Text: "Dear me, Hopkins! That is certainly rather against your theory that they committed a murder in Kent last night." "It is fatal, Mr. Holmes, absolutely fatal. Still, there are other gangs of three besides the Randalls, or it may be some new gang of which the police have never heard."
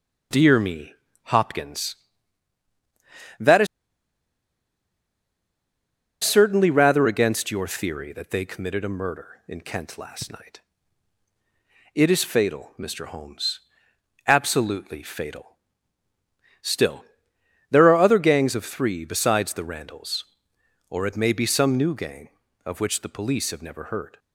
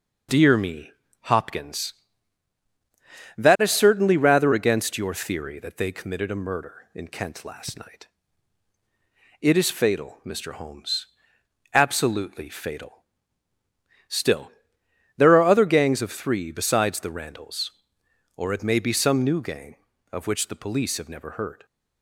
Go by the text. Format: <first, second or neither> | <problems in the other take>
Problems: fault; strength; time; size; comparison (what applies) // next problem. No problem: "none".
second | pauses between "is" and "certainly"; strong; at 3.6 s; 2.5 s long